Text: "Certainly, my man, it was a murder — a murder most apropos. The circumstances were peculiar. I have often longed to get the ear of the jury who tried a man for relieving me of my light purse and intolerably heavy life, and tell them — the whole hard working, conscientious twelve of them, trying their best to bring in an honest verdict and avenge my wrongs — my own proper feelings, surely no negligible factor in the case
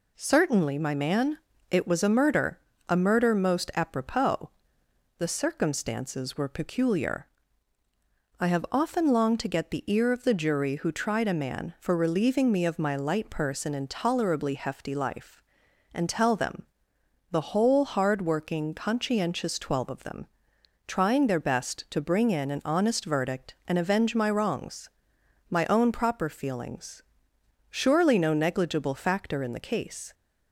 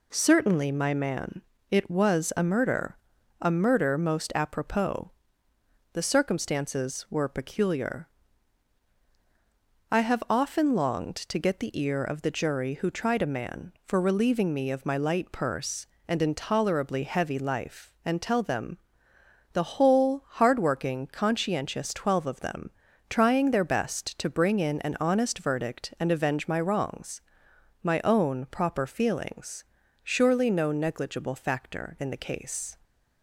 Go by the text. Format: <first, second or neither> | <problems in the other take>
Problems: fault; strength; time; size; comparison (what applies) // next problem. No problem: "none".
second | says "hefty" for "heavy"; at 14.5 s